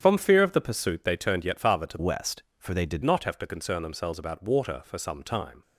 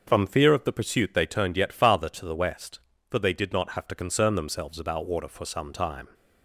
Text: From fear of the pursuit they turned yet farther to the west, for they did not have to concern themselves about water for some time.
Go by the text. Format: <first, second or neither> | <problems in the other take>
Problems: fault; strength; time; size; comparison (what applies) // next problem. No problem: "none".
second | starts louder than the rest; strong; until 1.0 s; 8.5 dB; also in the second // changes voice from "west" to "did"; from 1.9 to 3.0 s; 1.1 s long